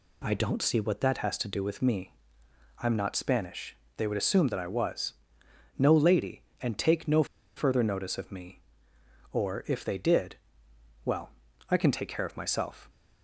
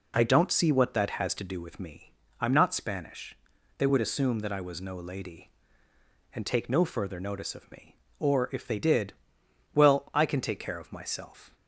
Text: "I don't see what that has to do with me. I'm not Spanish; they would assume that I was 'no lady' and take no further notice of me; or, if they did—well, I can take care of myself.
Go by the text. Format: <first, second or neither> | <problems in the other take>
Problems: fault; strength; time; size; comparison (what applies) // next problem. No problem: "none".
second | pauses between "was" and "no"; noticeable; at 5.1 s; 0.62 s long // pauses between "no" and "further"; slight; at 7.2 s; 0.31 s long